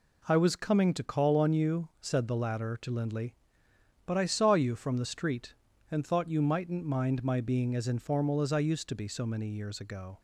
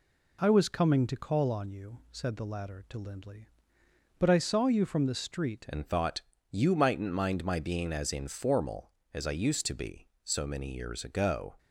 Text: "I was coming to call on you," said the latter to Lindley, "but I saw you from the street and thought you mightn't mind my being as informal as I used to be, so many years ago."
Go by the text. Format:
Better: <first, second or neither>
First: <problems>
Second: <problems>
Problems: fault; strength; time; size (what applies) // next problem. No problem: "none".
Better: first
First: none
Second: changes voice at "and"; from 5.6 s on; 5.9 s long // pauses between "thought" and "you"; slight; at 6.2 s; 0.28 s long